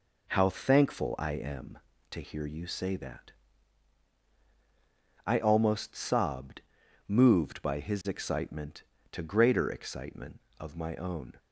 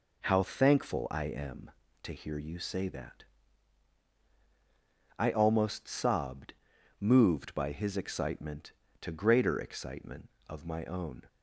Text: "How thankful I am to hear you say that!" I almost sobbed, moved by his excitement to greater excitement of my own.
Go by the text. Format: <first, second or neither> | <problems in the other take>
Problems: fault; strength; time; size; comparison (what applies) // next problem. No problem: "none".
neither | none